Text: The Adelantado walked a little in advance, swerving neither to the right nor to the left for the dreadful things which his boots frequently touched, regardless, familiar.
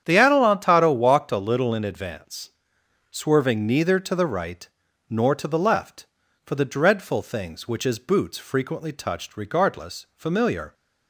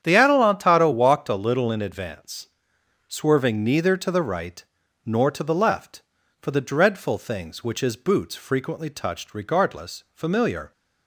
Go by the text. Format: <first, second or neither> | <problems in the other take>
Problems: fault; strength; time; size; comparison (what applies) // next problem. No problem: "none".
neither | starts louder than the rest; strong; the same in both // pauses between "right" and "nor"; the same in both